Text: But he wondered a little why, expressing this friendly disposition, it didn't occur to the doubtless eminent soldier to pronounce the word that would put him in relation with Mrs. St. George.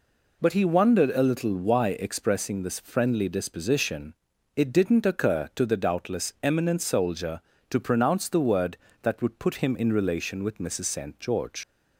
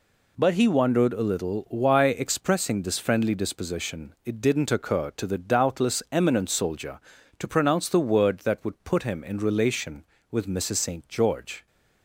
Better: second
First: leaves "George" unfinished; at 11.6 s; 85 ms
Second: none

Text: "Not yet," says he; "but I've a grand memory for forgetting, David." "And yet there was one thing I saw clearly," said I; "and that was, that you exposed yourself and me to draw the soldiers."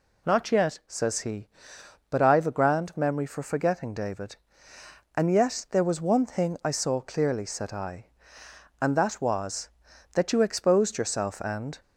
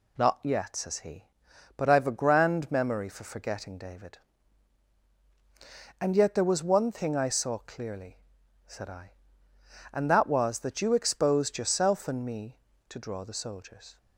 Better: second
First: stops before "me to draw the soldiers"; at 11.8 s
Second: none

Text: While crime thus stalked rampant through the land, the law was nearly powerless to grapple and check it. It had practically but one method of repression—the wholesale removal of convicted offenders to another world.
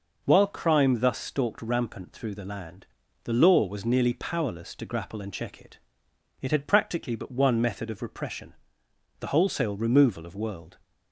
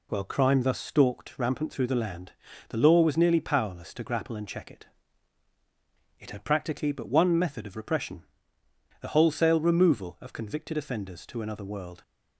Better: second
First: skips "convicted offenders to another"; at 10.3 s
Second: none

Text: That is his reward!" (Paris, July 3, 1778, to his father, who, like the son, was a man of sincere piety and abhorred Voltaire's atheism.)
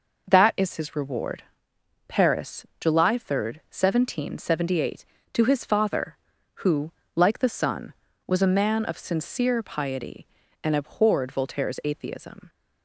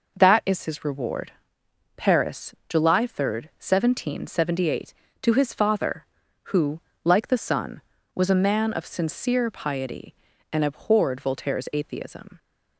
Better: neither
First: none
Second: none

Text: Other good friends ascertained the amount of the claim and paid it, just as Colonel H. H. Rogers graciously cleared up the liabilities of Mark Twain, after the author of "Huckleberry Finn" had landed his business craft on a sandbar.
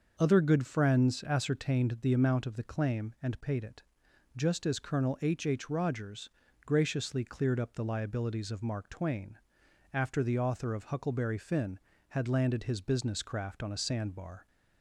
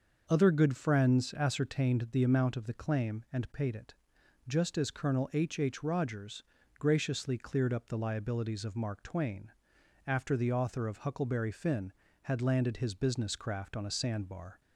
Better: neither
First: starts louder than the rest; until 1.1 s; 6.5 dB // pauses between "Rogers" and "graciously"; slight; at 6.2 s; 0.36 s long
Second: starts louder than the rest; until 1.2 s; 6.5 dB // pauses between "Rogers" and "graciously"; slight; at 6.4 s; 0.36 s long

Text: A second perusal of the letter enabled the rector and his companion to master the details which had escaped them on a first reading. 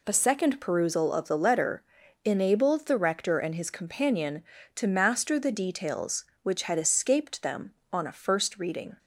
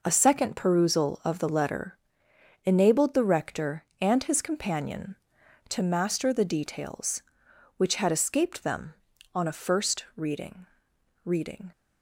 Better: first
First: pauses between "letter" and "enabled"; at 1.8 s; 0.44 s long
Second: pauses between "letter" and "enabled"; noticeable; at 1.9 s; 0.68 s long // says "reading" twice; at 11.2 s

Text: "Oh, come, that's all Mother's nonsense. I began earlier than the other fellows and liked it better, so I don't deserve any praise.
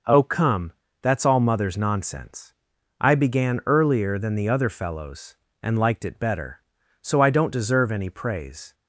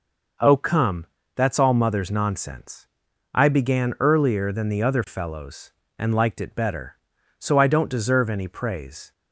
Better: neither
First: none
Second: none

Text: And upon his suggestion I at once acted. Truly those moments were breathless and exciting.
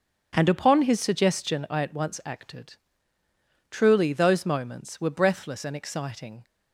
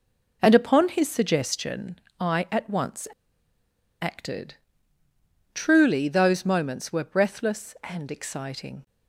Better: first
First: none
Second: pauses between "suggestion" and "I"; slight; at 1.9 s; 0.20 s long // pauses between "once" and "acted"; noticeable; at 3.0 s; 0.93 s long

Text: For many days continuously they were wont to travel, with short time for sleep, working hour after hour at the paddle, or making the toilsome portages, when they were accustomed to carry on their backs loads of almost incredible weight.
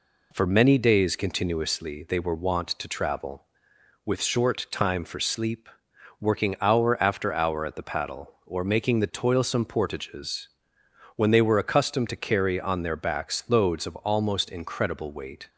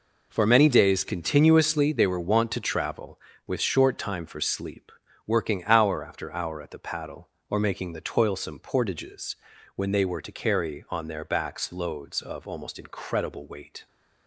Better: first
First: none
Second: skips "accustomed"; at 10.2 s

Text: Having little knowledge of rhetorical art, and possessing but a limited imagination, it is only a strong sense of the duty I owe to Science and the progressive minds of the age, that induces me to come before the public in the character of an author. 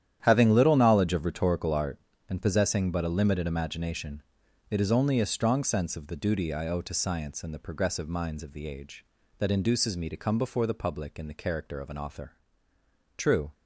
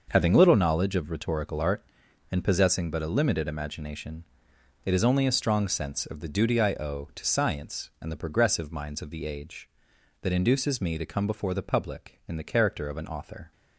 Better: second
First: starts louder than the rest; strong; until 1.2 s; 10.5 dB // goes on to say "True"; slight; from 13.1 s on; 0.34 s long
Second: starts louder than the rest; until 1.0 s; 6 dB

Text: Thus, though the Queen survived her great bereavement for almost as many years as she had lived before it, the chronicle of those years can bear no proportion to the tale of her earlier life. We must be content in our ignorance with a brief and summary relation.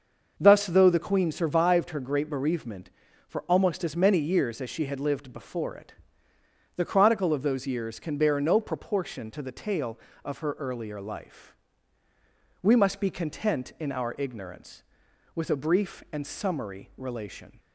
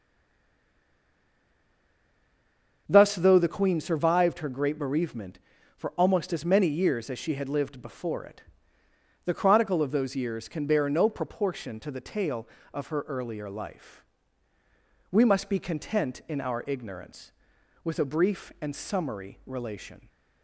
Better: first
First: starts louder than the rest; until 1.3 s; 6 dB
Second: stays silent before the first word; strong; until 2.8 s; 2.8 s long // starts louder than the rest; until 3.8 s; 6 dB

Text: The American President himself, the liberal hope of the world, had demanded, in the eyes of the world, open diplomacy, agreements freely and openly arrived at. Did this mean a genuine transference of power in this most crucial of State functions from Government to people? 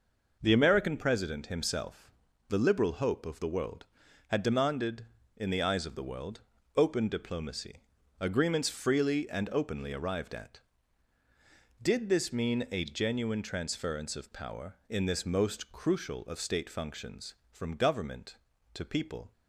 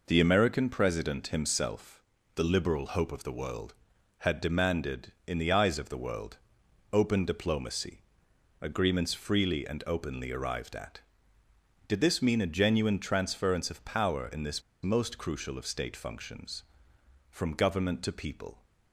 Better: first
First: none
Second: pauses between "this" and "most"; slight; at 14.6 s; 0.21 s long

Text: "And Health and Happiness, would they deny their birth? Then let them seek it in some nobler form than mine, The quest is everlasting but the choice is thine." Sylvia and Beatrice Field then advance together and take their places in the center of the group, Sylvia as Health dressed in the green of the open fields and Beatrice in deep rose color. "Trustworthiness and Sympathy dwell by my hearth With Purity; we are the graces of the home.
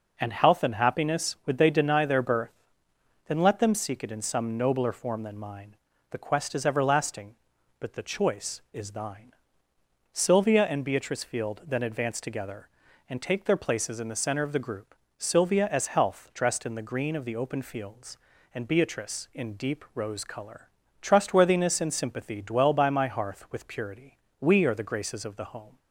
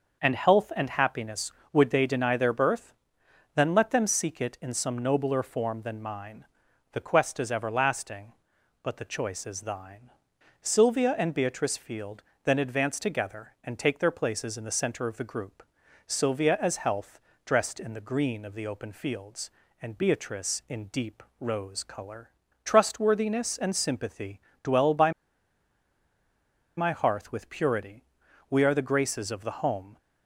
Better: first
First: none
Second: starts louder than the rest; until 1.2 s; 6.5 dB // pauses between "Field" and "then"; slight; at 12.2 s; 0.22 s long // pauses between "Health" and "dressed"; slight; at 17.2 s; 0.24 s long // pauses between "deep" and "rose"; slight; at 21.2 s; 0.16 s long // pauses between "Sympathy" and "dwell"; slight; at 24.4 s; 0.22 s long // pauses between "by" and "my"; strong; at 25.1 s; 1.6 s long

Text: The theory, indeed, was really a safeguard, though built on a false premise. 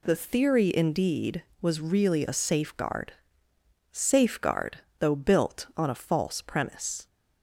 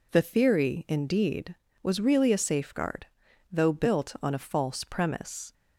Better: second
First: says "safeguard" twice; at 3.9 s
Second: none

